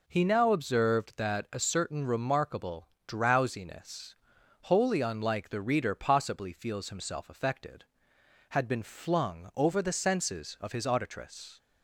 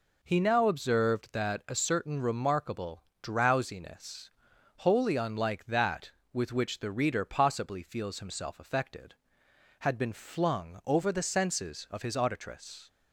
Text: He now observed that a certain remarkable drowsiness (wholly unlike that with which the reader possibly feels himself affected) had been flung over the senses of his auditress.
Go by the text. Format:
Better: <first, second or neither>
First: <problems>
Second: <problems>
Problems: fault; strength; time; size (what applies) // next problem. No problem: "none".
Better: second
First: pauses between "remarkable" and "drowsiness"; slight; at 2.8 s; 0.20 s long // skips "that with which"; at 5.4 s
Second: pauses between "remarkable" and "drowsiness"; slight; at 3.0 s; 0.20 s long